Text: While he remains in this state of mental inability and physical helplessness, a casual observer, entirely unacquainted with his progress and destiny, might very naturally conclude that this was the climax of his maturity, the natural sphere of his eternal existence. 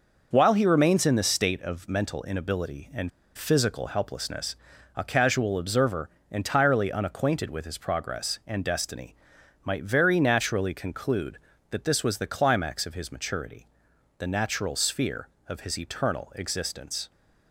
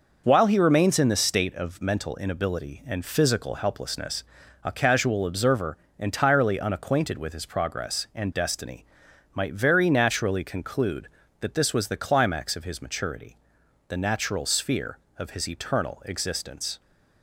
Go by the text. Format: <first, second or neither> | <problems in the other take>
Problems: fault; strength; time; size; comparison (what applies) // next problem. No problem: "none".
second | pauses between "and" and "physical"; slight; at 3.1 s; 0.26 s long